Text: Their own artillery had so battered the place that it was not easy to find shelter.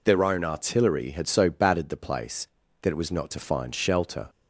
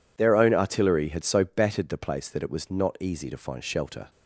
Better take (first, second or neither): second